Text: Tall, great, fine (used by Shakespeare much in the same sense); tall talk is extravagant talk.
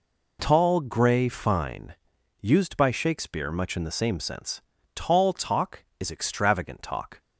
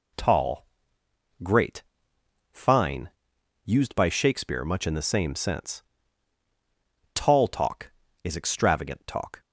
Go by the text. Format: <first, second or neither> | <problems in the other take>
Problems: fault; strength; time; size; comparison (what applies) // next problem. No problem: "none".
second | says "grey" for "great"; at 0.8 s